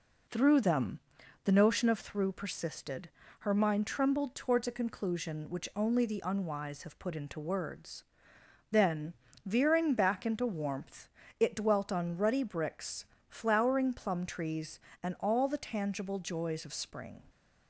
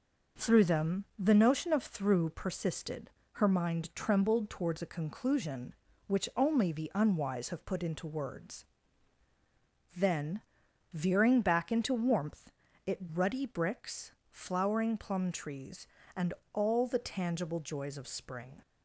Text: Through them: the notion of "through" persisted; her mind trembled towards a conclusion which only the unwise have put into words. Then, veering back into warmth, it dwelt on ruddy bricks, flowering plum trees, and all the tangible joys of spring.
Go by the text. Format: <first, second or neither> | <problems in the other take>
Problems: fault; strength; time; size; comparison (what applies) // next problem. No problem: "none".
first | skips "dwelt on"; at 13.1 s // pauses between "and" and "all"; slight; at 16.3 s; 0.22 s long